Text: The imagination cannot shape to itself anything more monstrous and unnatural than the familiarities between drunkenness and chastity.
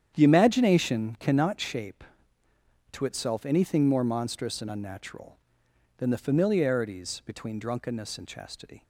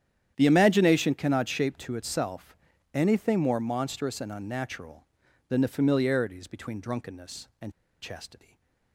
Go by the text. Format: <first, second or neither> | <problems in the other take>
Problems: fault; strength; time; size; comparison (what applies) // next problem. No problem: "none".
first | starts louder than the rest; strong; until 1.3 s; 10 dB; strong in the first // pauses between "itself" and "anything"; at 2.5 s; 0.38 s long // pauses between "and" and "chastity"; slight; at 7.7 s; 0.31 s long // stays silent after the last word; slight; from 8.4 s on; 0.5 s long